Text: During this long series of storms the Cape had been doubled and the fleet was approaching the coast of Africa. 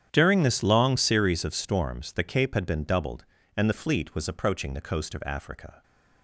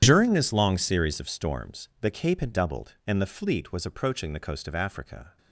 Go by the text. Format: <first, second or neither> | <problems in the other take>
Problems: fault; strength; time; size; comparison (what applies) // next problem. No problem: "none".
first | starts louder than the rest; strong; until 1.0 s; 10 dB; strong in the first // skips "been"; at 2.5 s